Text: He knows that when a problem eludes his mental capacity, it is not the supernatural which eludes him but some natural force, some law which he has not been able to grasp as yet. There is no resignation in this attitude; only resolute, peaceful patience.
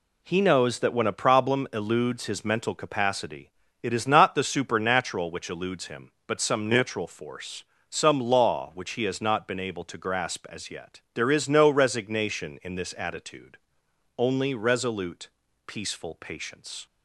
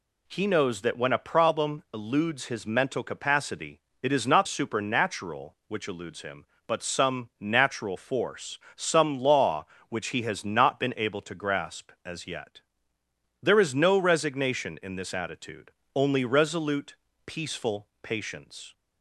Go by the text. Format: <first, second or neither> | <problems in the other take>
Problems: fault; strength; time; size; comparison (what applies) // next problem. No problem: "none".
first | skips "the"; at 4.4 s